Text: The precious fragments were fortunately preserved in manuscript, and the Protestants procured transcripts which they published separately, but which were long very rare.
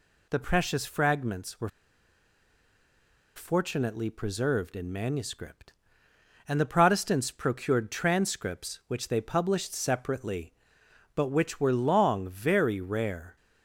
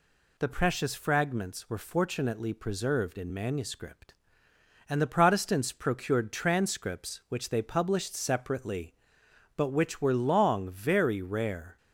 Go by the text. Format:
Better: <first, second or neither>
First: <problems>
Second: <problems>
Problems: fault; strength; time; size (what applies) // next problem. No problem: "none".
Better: second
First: pauses between "were" and "fortunately"; strong; at 1.6 s; 1.6 s long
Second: none